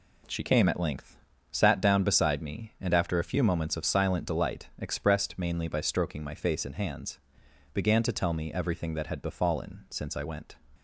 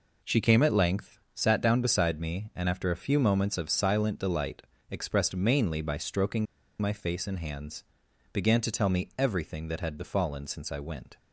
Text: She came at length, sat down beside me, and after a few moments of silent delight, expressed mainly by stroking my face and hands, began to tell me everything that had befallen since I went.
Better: first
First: none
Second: pauses between "stroking" and "my"; slight; at 6.4 s; 0.34 s long

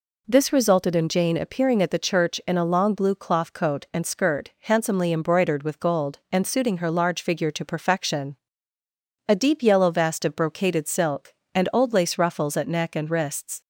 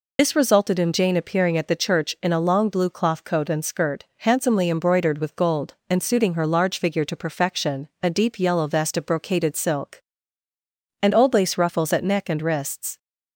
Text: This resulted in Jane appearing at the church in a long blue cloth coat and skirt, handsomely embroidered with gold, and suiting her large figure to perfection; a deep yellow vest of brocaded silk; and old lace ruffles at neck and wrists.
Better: first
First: none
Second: loses the start of "This"; at 0.1 s; 55 ms

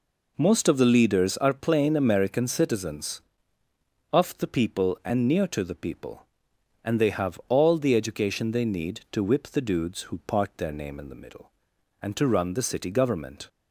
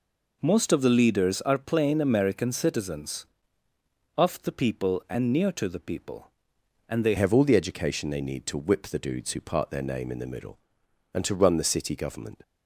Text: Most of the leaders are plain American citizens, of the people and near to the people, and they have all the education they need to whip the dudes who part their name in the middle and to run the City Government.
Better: first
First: none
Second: changes voice at "have"; from 7.1 s on; 5.3 s long

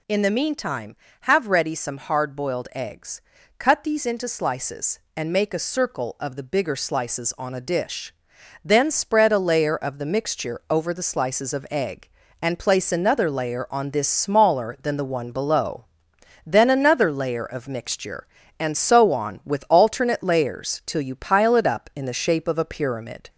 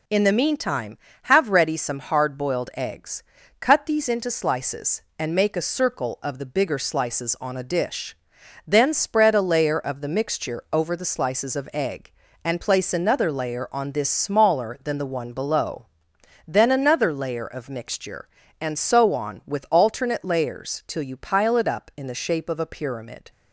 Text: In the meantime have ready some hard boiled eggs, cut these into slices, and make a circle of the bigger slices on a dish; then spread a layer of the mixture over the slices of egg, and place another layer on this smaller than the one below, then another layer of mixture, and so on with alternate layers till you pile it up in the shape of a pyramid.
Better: second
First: gets louder; slight; throughout; 3 dB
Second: none

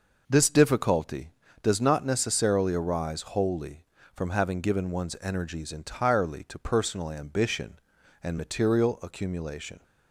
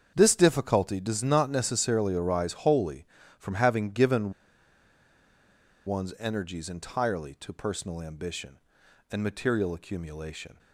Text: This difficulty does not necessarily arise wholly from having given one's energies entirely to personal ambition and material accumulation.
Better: first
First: none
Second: starts louder than the rest; until 1.1 s; 7 dB // pauses between "given" and "one's"; strong; at 4.3 s; 1.5 s long

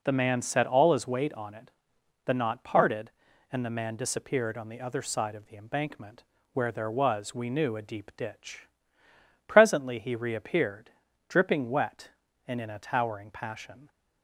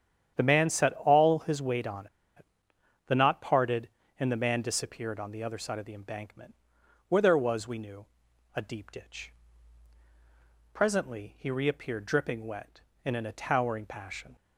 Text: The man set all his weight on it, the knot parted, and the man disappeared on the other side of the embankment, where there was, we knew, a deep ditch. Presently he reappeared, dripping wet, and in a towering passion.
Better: first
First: none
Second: starts louder than the rest; strong; until 1.3 s; 9.5 dB // pauses between "on" and "it"; slight; at 2.0 s; 0.30 s long

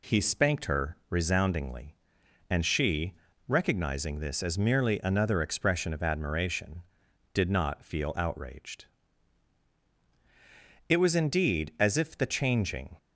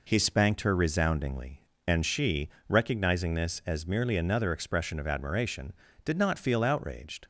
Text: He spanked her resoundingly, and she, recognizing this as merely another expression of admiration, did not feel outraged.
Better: second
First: goes on to say "It was indeed as if the changing"; strong; from 10.9 s on; 2.0 s long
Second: none

